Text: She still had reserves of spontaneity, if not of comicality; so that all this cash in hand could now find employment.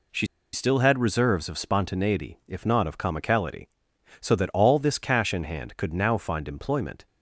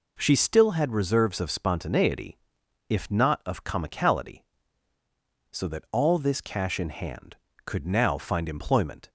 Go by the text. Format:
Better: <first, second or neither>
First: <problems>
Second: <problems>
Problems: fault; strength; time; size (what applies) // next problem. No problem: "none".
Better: second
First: pauses between "She" and "still"; slight; at 0.2 s; 0.27 s long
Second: none